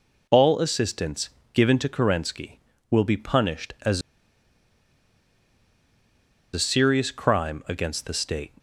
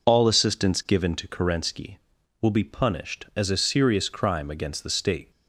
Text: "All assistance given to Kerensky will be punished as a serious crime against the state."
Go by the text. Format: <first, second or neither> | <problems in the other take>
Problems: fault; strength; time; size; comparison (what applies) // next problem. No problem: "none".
second | pauses between "assistance" and "given"; slight; at 1.2 s; 0.24 s long // pauses between "as" and "a"; strong; at 4.0 s; 2.5 s long